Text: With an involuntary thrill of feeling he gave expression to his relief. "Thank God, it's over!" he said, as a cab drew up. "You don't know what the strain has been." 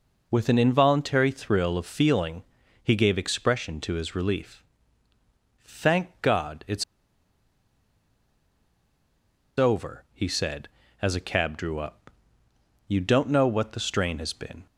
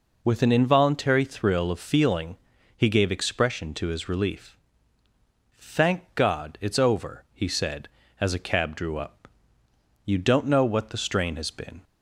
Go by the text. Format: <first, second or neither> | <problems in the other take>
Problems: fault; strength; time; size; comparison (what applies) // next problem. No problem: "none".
second | pauses between "feeling" and "he"; at 2.4 s; 0.40 s long; also in the second // pauses between "it's" and "over"; strong; at 6.8 s; 2.7 s long